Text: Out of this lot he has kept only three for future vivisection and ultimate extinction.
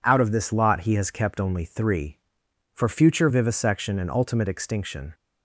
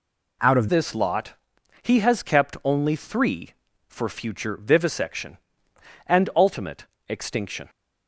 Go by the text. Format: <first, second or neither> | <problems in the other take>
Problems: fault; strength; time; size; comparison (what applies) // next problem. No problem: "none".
first | changes voice at "this"; from 0.6 s on; 7.0 s long // pauses between "lot" and "he"; noticeable; at 1.3 s; 0.48 s long // pauses between "ultimate" and "extinction"; slight; at 6.8 s; 0.22 s long